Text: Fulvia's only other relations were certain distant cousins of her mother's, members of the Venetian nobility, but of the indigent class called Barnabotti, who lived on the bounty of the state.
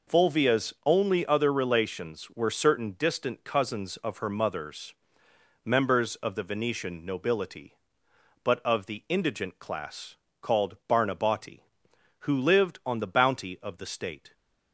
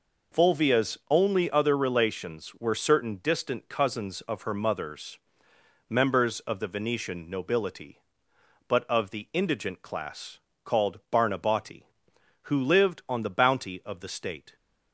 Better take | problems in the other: neither | pauses between "class" and "called"; slight; the same in both

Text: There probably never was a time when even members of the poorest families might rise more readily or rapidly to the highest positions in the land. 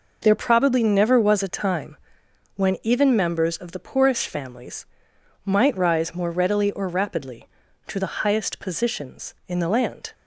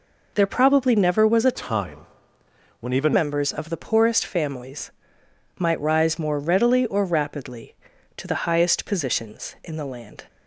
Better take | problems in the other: first | changes voice from "time" to "even"; from 1.5 to 3.1 s; 1.6 s long // pauses between "time" and "when"; noticeable; at 1.9 s; 0.82 s long; noticeable in the first // pauses between "families" and "might"; noticeable; at 4.9 s; 0.68 s long; noticeable in the first

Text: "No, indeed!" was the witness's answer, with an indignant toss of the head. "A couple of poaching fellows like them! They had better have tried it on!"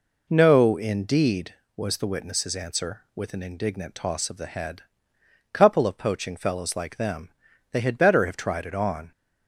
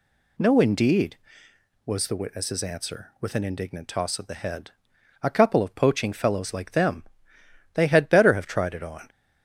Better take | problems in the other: second | skips "A"; at 5.1 s

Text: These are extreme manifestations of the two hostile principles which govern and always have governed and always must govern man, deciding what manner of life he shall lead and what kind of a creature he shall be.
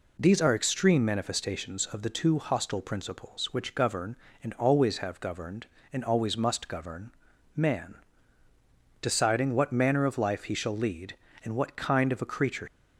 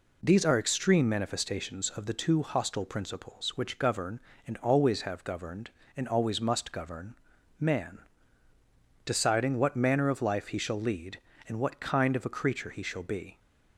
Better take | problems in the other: second | pauses between "govern" and "man"; at 7.1 s; 0.44 s long; also in the second // stops before "he shall be"; at 12.6 s

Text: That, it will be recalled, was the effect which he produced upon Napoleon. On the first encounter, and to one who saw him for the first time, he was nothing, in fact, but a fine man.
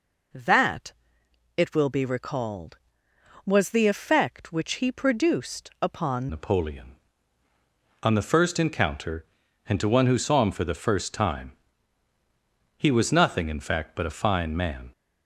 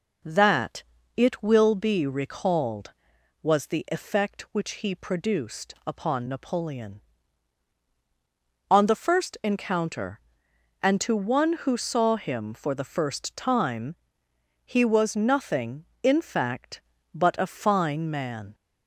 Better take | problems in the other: second | changes voice at "Napoleon"; from 6.2 s on; 8.7 s long

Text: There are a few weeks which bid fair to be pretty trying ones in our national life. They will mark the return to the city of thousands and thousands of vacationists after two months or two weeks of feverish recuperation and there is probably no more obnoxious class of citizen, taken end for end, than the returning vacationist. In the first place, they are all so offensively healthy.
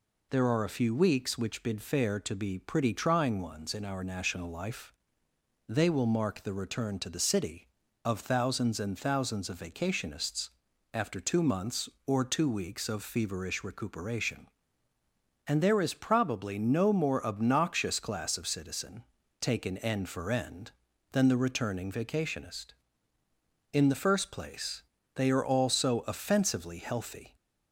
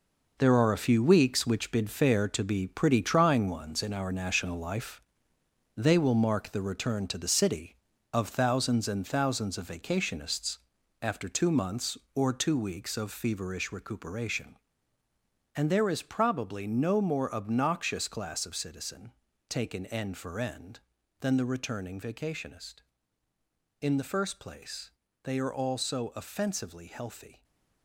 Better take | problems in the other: first | gets quieter; strong; throughout; 9 dB // pauses between "vacationists" and "after"; at 10.5 s; 0.42 s long; also in the first

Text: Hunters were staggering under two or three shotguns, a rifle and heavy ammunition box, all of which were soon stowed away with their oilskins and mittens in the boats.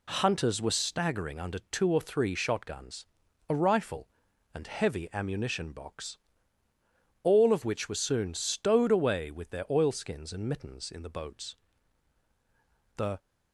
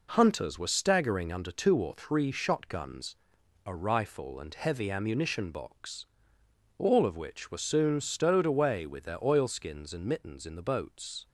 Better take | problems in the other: second | goes on to say "The"; slight; from 12.9 s on; 0.22 s long

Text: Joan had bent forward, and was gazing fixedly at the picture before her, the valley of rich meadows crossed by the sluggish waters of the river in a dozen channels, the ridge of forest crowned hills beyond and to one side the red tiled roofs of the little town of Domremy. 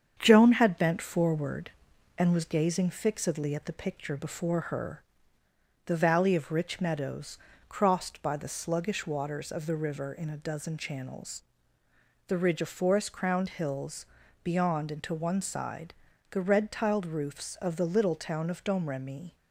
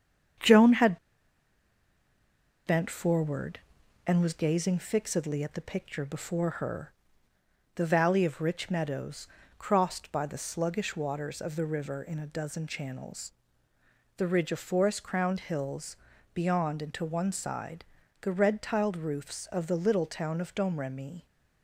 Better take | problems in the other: first | starts louder than the rest; strong; until 3.0 s; 7.5 dB; strong in the first // pauses between "had" and "bent"; strong; at 0.9 s; 1.6 s long // pauses between "meadows" and "crossed"; slight; at 9.2 s; 0.32 s long; slight in the first // pauses between "hills" and "beyond"; at 15.9 s; 0.40 s long; also in the first // pauses between "side" and "the"; at 17.8 s; 0.38 s long; also in the first

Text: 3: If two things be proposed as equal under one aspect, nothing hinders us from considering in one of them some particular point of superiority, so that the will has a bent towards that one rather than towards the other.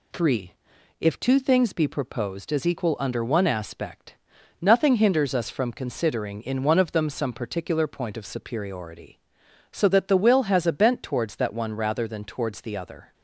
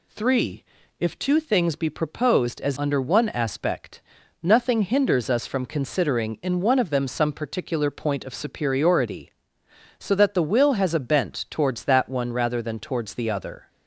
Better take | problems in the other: first | skips "equal"; at 2.7 s

